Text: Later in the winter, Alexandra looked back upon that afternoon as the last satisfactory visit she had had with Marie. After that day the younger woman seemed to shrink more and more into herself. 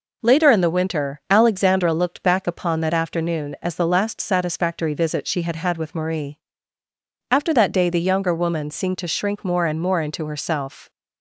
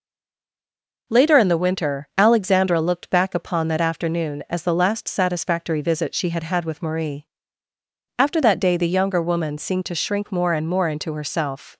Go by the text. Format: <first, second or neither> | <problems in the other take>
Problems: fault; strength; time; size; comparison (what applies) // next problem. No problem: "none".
first | stays silent before the first word; until 1.0 s; 1.0 s long